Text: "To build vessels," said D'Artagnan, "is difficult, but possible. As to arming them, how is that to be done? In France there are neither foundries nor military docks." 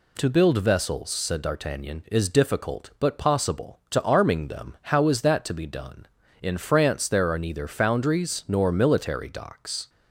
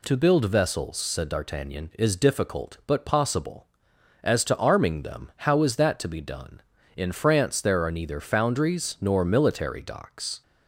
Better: second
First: skips "As"; at 3.8 s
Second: none

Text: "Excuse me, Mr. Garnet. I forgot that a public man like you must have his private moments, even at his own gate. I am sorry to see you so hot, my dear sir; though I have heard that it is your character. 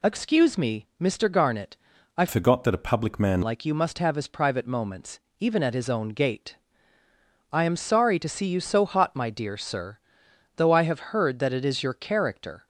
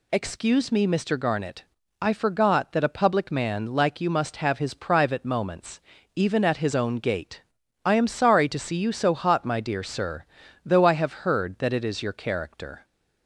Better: second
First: changes voice from "forgot" to "man"; from 2.2 to 3.4 s; 1.2 s long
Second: none

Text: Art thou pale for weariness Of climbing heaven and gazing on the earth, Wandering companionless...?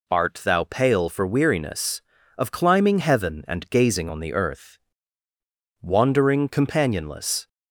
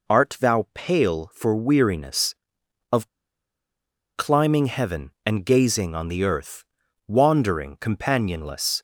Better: first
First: none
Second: pauses between "Of" and "climbing"; at 3.0 s; 1.0 s long

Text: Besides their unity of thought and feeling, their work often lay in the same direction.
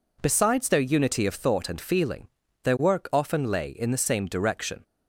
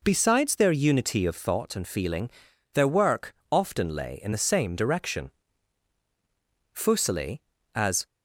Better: first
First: none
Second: pauses between "work" and "often"; slight; at 3.3 s; 0.18 s long // goes on to say "Fuseli as"; from 6.7 s on; 1.3 s long

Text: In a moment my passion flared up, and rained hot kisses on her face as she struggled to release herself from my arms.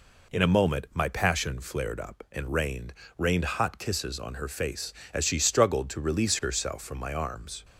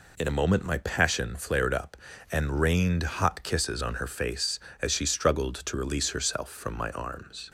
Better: second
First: says "rained" twice; at 3.1 s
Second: none

